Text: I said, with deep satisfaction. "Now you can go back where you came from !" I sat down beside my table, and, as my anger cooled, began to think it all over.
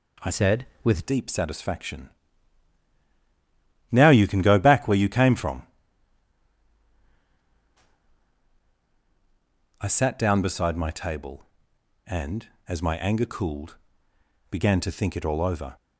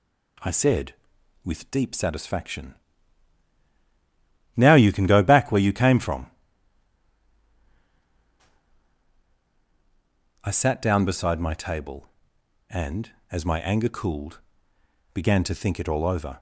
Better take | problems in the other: second | changes voice from "said" to "with"; from 0.3 to 1.0 s; 0.7 s long

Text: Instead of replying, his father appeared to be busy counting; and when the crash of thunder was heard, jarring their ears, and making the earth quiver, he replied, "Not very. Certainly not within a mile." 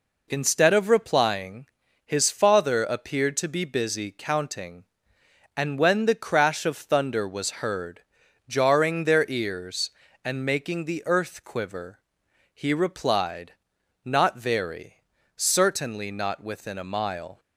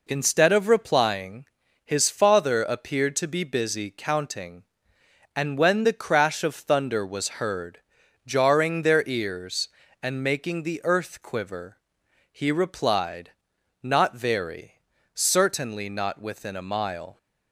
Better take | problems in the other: neither | none

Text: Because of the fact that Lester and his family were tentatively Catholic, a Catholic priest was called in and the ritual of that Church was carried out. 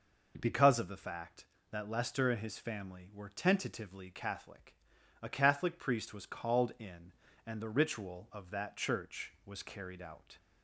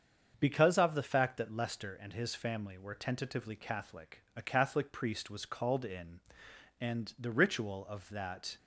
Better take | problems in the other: first | starts louder than the rest; until 1.4 s; 7 dB // stops before "Church was carried out"; at 8.5 s

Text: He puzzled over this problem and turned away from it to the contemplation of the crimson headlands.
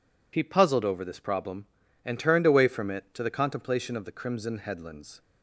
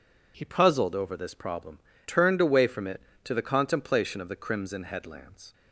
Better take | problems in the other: first | skips "and"; at 1.9 s

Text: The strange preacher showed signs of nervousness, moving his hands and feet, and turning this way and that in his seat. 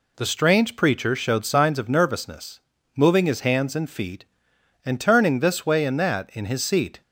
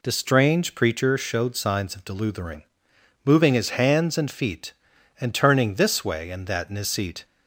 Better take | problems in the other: first | says "deluthering" for "nervousness"; at 2.0 s

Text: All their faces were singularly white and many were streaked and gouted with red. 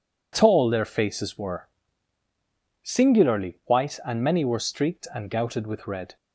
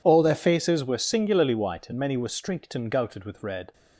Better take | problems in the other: second | says "Tall" for "All"; at 0.3 s // pauses between "were" and "singularly"; at 1.6 s; 1.1 s long

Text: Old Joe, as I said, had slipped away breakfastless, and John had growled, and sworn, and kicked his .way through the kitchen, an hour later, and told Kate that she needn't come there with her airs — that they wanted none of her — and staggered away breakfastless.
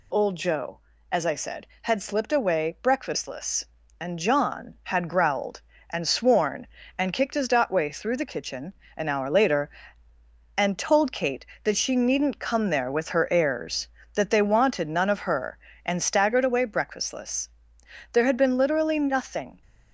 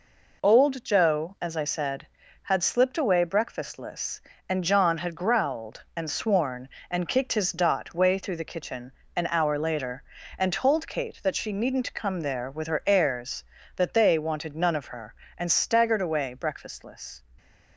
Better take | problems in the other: second | goes on to say "There had been literally nothing"; from 18.1 s on; 1.5 s long

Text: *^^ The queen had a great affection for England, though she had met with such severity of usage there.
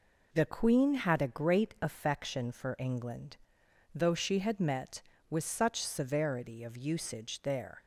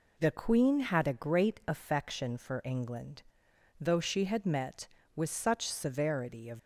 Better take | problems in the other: first | stops before "usage there"; at 6.5 s

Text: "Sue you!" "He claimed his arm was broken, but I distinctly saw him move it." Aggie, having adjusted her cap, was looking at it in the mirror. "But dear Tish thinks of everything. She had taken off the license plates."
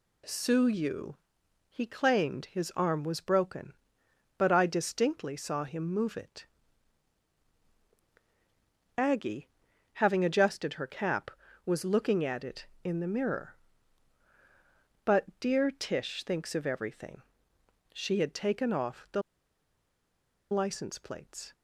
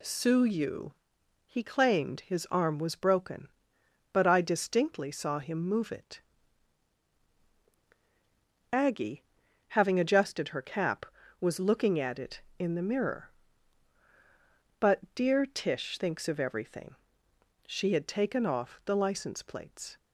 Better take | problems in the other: second | pauses between "the" and "license"; strong; at 19.2 s; 1.3 s long

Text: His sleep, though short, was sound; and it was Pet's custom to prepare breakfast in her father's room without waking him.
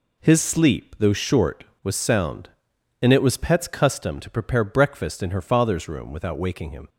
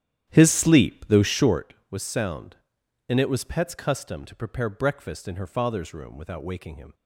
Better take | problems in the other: first | starts louder than the rest; strong; until 1.7 s; 11 dB

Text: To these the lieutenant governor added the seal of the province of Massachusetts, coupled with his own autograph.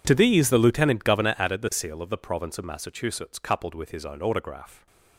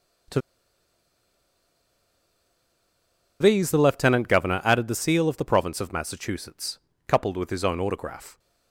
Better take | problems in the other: first | pauses between "To" and "these"; strong; at 0.3 s; 3.0 s long

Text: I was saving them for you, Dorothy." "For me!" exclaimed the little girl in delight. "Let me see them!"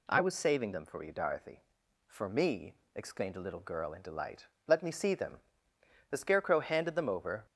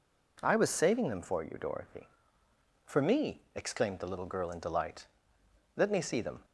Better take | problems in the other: second | goes on to say "The Scarecrow handed them over"; from 6.0 s on; 1.3 s long

